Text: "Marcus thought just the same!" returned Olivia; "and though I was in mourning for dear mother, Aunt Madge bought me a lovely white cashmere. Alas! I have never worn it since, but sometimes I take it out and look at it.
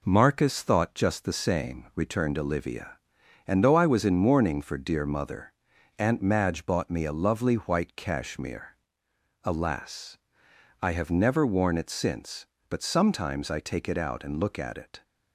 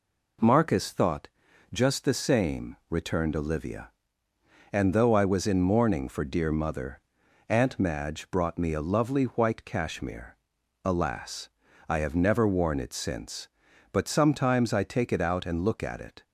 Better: first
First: none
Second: pauses between "thought" and "just"; noticeable; at 1.2 s; 0.46 s long // says "brought" for "bought"; at 8.2 s

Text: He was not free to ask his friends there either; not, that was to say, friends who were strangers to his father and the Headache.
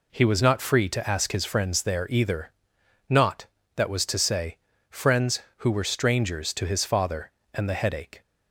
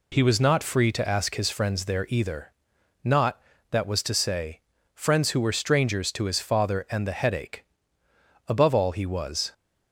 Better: first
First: none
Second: goes on to say "Above all he was"; noticeable; from 8.4 s on; 1.0 s long

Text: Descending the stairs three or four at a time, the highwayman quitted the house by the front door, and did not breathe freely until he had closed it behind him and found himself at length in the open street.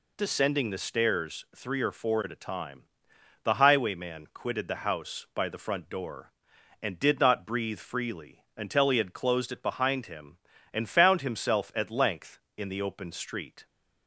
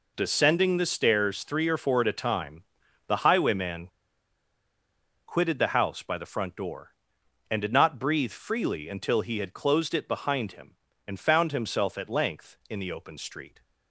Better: first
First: none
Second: pauses between "highwayman" and "quitted"; strong; at 3.8 s; 1.3 s long

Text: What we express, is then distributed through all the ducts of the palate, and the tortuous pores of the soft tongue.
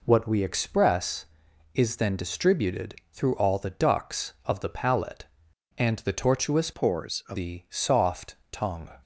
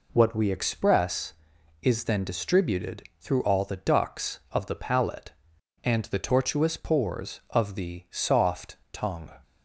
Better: second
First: pauses between "distributed" and "through"; slight; at 2.9 s; 0.18 s long // changes voice from "pores" to "of"; from 6.7 to 7.3 s; 0.6 s long // pauses between "soft" and "tongue"; slight; at 8.3 s; 0.16 s long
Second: pauses between "distributed" and "through"; slight; at 3.0 s; 0.18 s long // pauses between "soft" and "tongue"; slight; at 8.7 s; 0.16 s long

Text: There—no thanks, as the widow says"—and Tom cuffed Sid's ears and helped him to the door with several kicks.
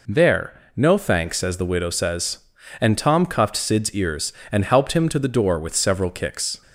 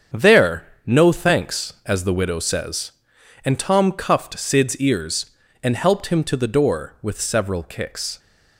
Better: first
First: none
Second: gets quieter; strong; throughout; 8 dB

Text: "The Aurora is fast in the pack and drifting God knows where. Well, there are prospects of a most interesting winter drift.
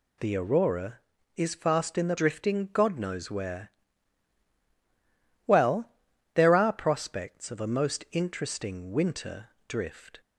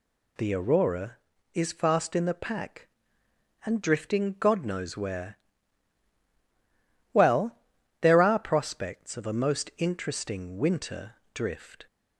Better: second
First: skips "pack and"; at 2.1 s // pauses between "winter" and "drift"; slight; at 9.4 s; 0.18 s long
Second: pauses between "winter" and "drift"; slight; at 11.1 s; 0.18 s long

